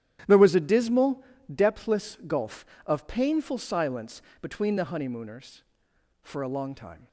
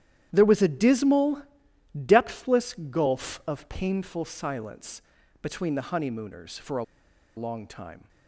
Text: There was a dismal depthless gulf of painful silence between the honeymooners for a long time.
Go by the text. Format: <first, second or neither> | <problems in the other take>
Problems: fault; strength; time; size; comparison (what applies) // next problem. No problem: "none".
first | starts louder than the rest; strong; until 1.3 s; 11 dB; strong in the first // pauses between "dismal" and "depthless"; noticeable; at 1.4 s; 0.62 s long; slight in the first // pauses between "depthless" and "gulf"; slight; at 2.7 s; 0.16 s long // pauses between "silence" and "between"; at 5.0 s; 0.40 s long; slight in the first // pauses between "a" and "long"; noticeable; at 6.8 s; 0.52 s long